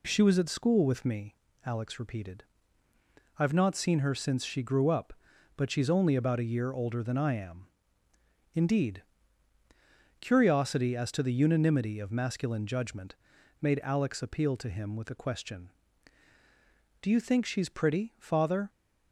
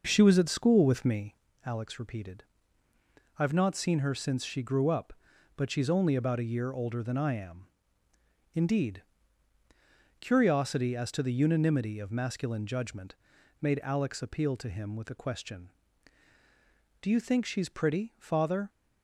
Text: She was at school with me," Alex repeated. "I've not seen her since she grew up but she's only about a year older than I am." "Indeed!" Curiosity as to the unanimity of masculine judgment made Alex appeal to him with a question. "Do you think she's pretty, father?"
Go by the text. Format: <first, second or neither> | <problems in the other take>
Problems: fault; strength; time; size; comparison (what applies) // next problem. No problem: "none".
first | starts louder than the rest; noticeable; until 1.5 s; 5.5 dB // pauses between "judgment" and "made"; at 13.1 s; 0.44 s long; also in the first